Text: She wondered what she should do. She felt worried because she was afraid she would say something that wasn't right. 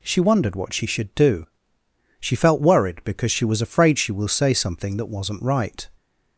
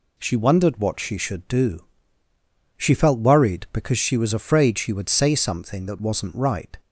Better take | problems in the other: second | says "will" for "would"; at 4.1 s

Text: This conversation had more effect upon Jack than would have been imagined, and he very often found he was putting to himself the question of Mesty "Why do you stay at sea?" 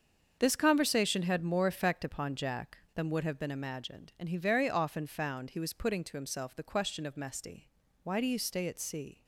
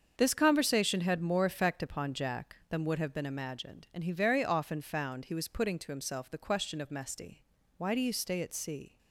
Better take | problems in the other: neither | starts louder than the rest; the same in both // pauses between "Mesty" and "Why"; slight; the same in both

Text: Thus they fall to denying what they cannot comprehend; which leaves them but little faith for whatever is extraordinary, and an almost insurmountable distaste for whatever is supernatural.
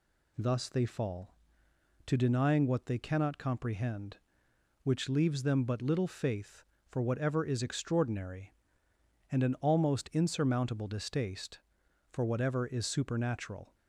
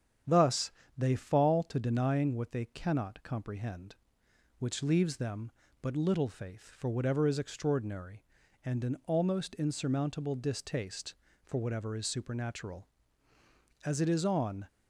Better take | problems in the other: first | starts louder than the rest; strong; until 1.5 s; 8.5 dB // pauses between "Thus" and "they"; slight; at 0.7 s; 0.26 s long // goes on to say "As it is on"; noticeable; from 13.8 s on; 0.86 s long

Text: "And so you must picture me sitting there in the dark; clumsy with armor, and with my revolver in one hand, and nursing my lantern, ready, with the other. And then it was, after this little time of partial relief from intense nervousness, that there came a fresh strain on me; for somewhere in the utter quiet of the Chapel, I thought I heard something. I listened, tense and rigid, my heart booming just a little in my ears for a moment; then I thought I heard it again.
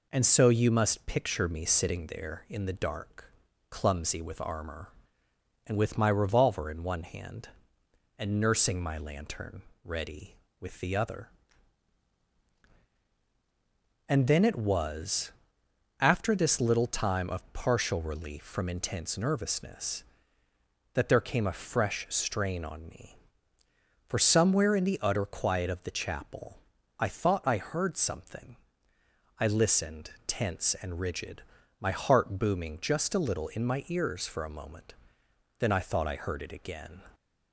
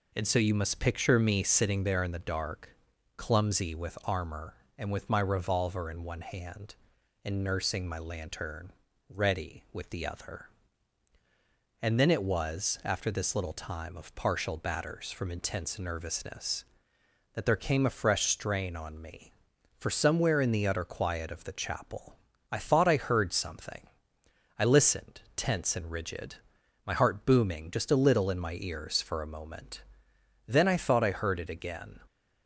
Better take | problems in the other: first | says "batters" for "relief"; at 14.5 s

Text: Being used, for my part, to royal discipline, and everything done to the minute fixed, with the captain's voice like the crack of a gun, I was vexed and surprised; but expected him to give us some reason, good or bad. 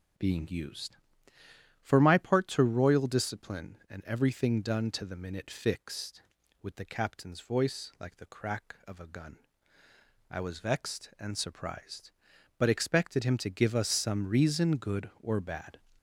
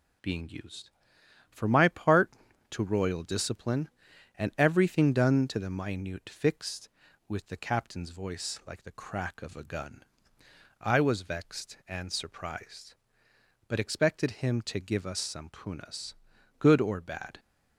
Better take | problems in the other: first | says "punas" for "reason"; at 15.5 s

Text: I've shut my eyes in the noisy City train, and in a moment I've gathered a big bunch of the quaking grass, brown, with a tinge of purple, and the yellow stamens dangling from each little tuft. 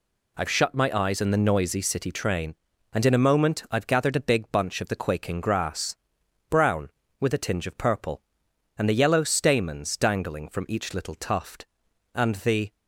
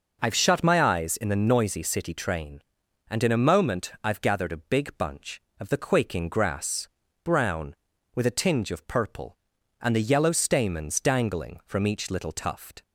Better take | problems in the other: second | goes on to say "And the"; from 12.1 s on; 0.60 s long

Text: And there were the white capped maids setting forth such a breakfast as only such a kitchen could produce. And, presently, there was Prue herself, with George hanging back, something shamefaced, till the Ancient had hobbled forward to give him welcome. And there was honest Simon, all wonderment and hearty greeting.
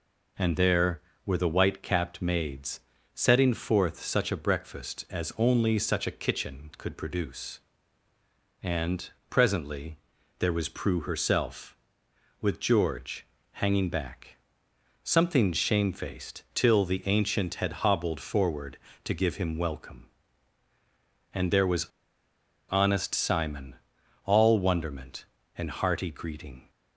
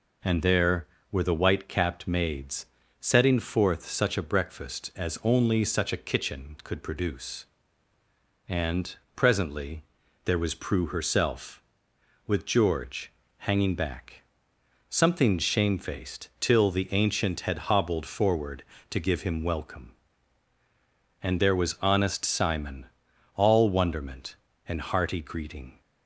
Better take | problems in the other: second | pauses between "maids" and "setting"; slight; at 2.7 s; 0.34 s long; slight in the second // pauses between "George" and "hanging"; slight; at 13.2 s; 0.24 s long; slight in the second // pauses between "was" and "honest"; noticeable; at 21.8 s; 0.86 s long

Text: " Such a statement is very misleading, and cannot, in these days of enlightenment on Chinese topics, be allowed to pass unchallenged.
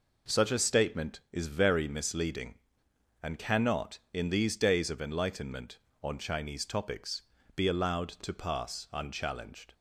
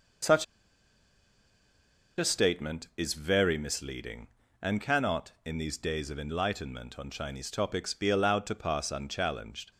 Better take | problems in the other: first | pauses between "Such" and "a"; strong; at 0.4 s; 1.7 s long

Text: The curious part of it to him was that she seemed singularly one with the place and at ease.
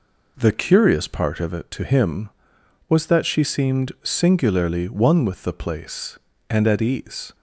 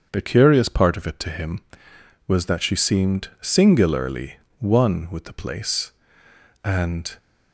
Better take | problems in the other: first | starts louder than the rest; until 1.1 s; 6.5 dB // pauses between "singularly" and "one"; slight; at 4.3 s; 0.22 s long // stops before "at ease"; at 7.1 s

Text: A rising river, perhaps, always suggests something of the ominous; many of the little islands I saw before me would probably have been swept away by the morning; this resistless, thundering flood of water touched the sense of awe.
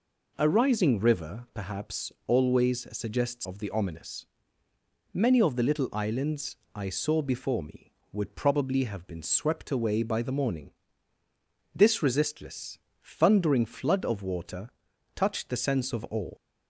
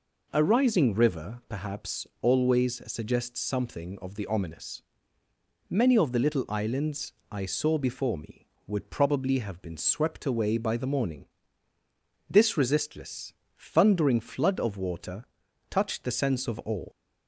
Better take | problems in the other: second | skips "something"; at 3.4 s // pauses between "islands" and "I"; slight; at 6.5 s; 0.18 s long; slight in the second // pauses between "water" and "touched"; noticeable; at 14.6 s; 0.48 s long; noticeable in the second

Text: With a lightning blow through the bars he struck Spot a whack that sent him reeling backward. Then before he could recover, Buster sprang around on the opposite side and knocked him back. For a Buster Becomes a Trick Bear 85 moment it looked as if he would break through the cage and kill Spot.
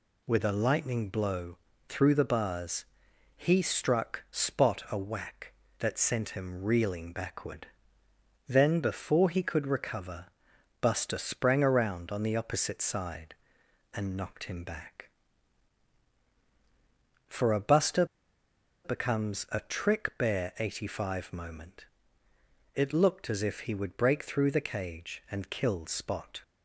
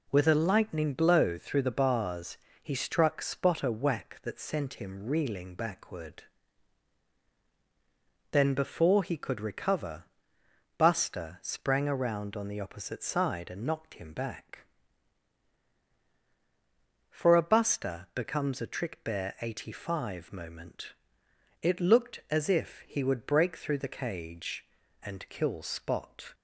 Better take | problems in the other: second | pauses between "blow" and "through"; slight; at 1.5 s; 0.32 s long // pauses between "bars" and "he"; noticeable; at 2.8 s; 0.52 s long; slight in the second // pauses between "Buster" and "Becomes"; noticeable; at 18.0 s; 0.79 s long // pauses between "moment" and "it"; noticeable; at 21.8 s; 0.90 s long; noticeable in the second

